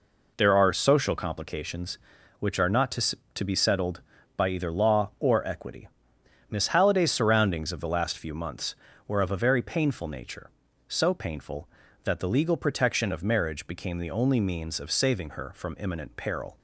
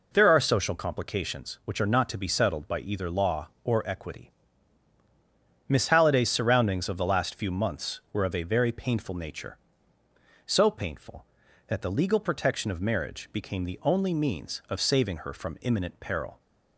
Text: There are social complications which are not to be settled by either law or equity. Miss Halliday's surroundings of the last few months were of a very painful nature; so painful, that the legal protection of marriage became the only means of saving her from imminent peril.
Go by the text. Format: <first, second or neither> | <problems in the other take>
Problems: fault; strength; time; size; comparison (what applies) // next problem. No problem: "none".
second | says "to" twice; at 3.3 s